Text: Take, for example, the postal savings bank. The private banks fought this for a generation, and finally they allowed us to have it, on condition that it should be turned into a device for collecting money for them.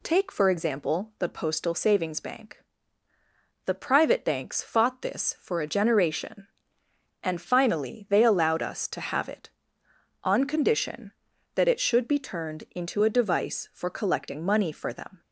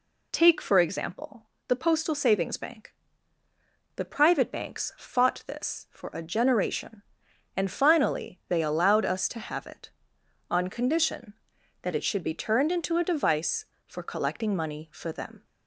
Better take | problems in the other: neither | none

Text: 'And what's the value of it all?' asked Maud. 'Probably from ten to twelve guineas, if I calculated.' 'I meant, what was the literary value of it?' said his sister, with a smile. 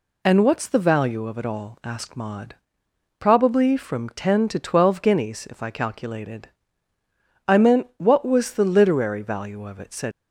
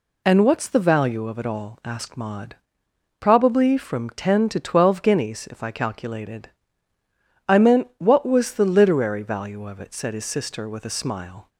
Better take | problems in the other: second | stops before "his sister with a smile"; at 10.1 s

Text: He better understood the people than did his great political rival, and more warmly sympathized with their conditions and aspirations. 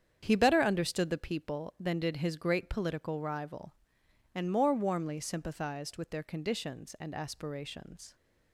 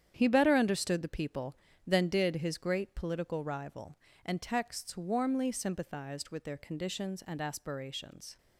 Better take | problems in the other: first | starts louder than the rest; strong; until 1.1 s; 9 dB; strong in the first // says "texts" for "more"; at 4.4 s

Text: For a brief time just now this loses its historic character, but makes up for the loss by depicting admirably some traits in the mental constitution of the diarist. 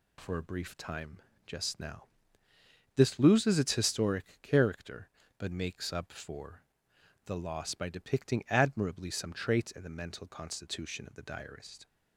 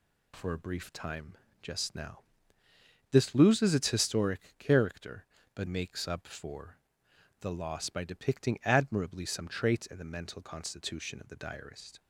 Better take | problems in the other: neither | pauses between "time" and "just"; slight; the same in both // pauses between "now" and "this"; noticeable; the same in both // pauses between "historic" and "character"; slight; the same in both // pauses between "for" and "the"; noticeable; the same in both

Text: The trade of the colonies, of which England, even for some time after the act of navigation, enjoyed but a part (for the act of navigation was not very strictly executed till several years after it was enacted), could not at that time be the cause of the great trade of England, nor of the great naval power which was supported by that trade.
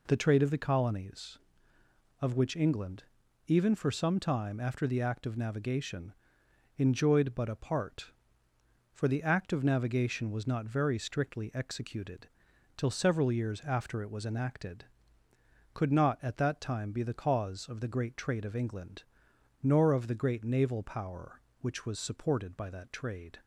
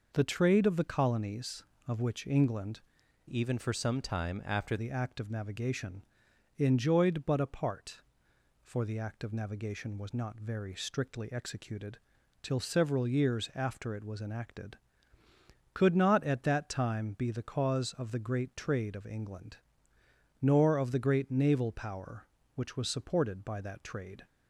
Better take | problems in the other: first | changes voice from "even" to "after"; from 3.2 to 4.7 s; 1.5 s long // pauses between "executed" and "till"; at 11.9 s; 0.44 s long; noticeable in the first

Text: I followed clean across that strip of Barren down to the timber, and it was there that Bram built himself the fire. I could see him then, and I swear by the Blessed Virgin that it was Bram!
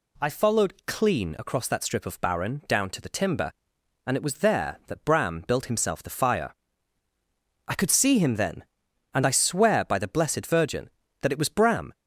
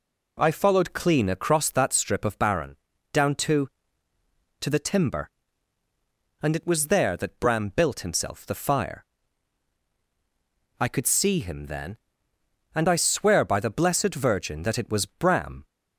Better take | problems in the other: first | pauses between "Barren" and "down"; slight; at 2.7 s; 0.36 s long // says "to" twice; at 4.6 s

